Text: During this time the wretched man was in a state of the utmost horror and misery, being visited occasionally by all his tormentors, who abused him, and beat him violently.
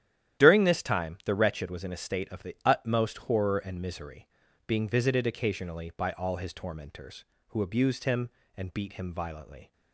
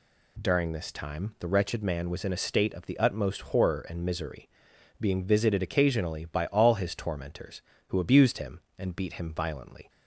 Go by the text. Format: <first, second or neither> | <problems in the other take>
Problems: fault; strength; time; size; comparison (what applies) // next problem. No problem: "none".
second | starts louder than the rest; strong; until 1.4 s; 11.5 dB // skips "man"; at 1.6 s